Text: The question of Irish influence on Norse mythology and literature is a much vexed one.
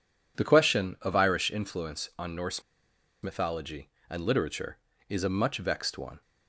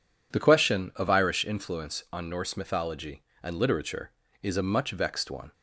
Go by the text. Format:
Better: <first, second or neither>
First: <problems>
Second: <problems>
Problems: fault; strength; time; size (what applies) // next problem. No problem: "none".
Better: second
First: pauses between "Norse" and "mythology"; noticeable; at 2.6 s; 0.60 s long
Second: none